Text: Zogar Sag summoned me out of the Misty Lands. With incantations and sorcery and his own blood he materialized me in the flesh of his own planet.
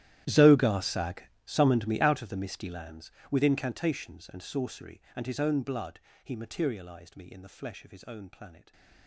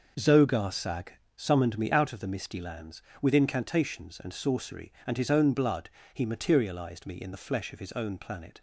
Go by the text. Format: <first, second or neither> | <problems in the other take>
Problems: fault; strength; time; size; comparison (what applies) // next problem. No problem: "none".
second | gets quieter; strong; throughout; 20.5 dB // pauses between "Sag" and "summoned"; slight; at 1.2 s; 0.23 s long; slight in the second // pauses between "blood" and "he"; slight; at 5.9 s; 0.26 s long; slight in the second